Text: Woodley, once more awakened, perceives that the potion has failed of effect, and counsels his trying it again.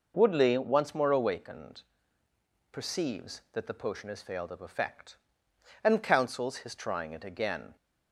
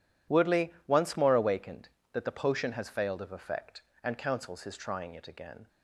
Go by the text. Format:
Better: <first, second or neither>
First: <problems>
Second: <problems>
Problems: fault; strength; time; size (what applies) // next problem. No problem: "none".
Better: first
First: none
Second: skips "perceives"; at 1.9 s